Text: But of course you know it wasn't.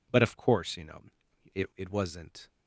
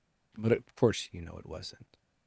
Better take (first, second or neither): second